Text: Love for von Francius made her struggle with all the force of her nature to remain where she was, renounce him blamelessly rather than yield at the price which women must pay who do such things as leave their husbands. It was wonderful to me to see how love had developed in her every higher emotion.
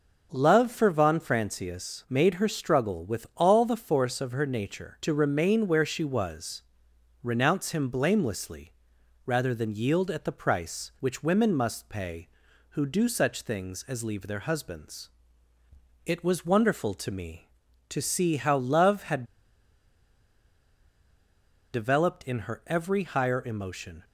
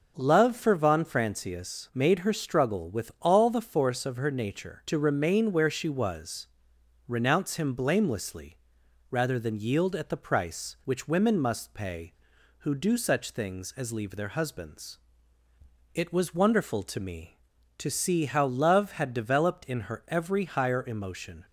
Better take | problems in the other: second | pauses between "blamelessly" and "rather"; noticeable; at 8.7 s; 0.56 s long; noticeable in the second // pauses between "had" and "developed"; strong; at 19.2 s; 2.4 s long

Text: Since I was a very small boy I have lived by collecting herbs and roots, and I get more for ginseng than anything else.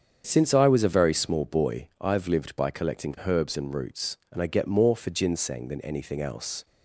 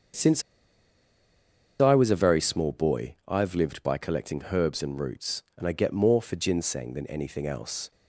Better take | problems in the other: first | starts louder than the rest; strong; until 2.5 s; 7 dB; strong in the first // pauses between "Since" and "I"; strong; at 0.4 s; 1.4 s long

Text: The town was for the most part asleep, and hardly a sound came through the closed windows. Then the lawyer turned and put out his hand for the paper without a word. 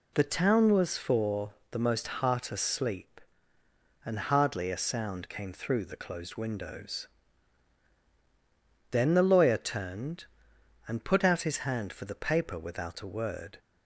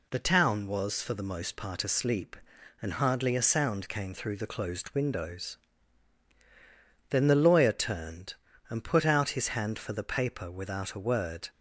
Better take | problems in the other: second | pauses between "for" and "the"; slight; at 1.5 s; 0.16 s long // says "heart" for "part"; at 2.0 s

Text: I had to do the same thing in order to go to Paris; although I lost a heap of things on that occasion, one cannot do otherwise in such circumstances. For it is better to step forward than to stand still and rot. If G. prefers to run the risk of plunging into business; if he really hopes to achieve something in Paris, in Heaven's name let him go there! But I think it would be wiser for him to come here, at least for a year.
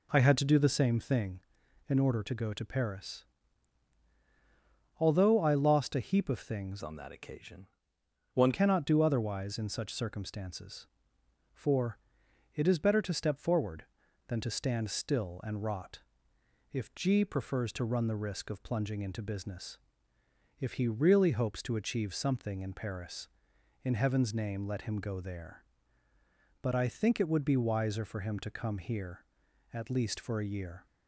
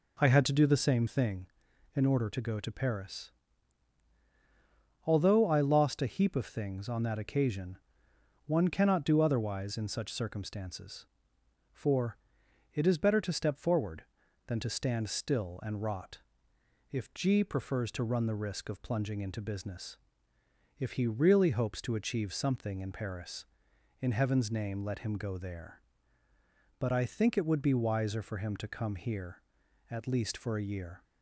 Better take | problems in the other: second | changes voice from "on" to "one"; from 6.8 to 8.5 s; 1.7 s long // pauses between "For" and "it"; noticeable; at 11.9 s; 0.56 s long; noticeable in the second

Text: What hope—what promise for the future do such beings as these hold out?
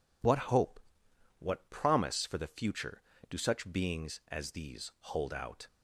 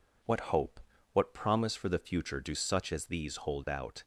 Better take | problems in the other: first | skips "beings"; at 2.9 s

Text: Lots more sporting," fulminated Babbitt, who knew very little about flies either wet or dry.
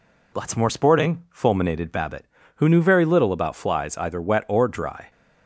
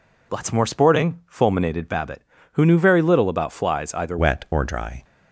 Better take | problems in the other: first | changes voice at "wet"; from 4.1 s on; 0.9 s long

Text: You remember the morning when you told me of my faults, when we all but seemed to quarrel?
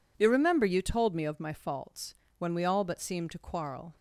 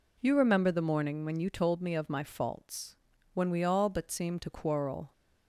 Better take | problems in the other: second | skips "the morning when"; at 0.6 s

